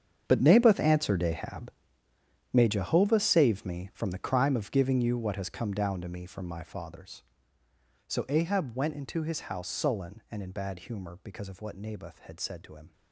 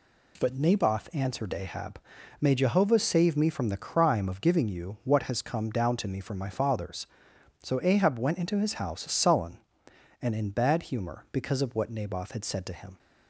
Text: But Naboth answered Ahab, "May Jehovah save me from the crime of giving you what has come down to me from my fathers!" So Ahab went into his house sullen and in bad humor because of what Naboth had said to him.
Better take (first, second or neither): second